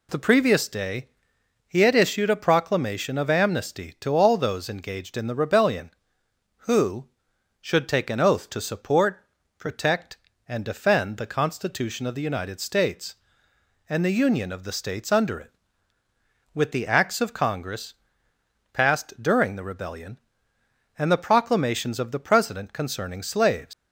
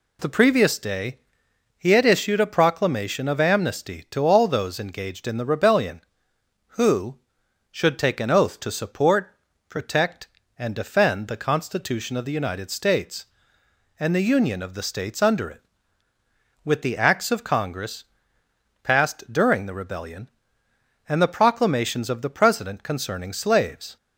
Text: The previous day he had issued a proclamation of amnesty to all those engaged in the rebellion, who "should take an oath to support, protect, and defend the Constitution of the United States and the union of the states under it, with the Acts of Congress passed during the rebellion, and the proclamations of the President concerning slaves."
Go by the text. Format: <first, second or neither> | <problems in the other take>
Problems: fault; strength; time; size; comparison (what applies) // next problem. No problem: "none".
second | pauses between "day" and "he"; noticeable; at 1.0 s; 0.60 s long; noticeable in the second // pauses between "Congress" and "passed"; noticeable; at 17.9 s; 0.78 s long; noticeable in the second // leaves "slaves" unfinished; at 23.7 s; 125 ms